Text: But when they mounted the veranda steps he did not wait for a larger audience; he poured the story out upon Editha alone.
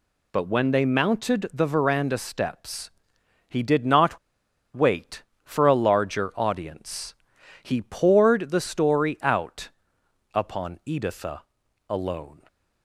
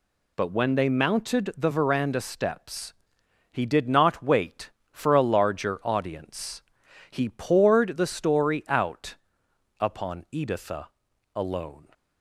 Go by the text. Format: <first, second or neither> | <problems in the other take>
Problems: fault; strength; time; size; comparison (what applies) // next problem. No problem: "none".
second | pauses between "steps" and "he"; noticeable; at 2.8 s; 0.58 s long; noticeable in the second // pauses between "not" and "wait"; noticeable; at 4.1 s; 0.56 s long // pauses between "out" and "upon"; noticeable; at 9.6 s; 0.66 s long; noticeable in the second // pauses between "Editha" and "alone"; noticeable; at 11.4 s; 0.48 s long; noticeable in the second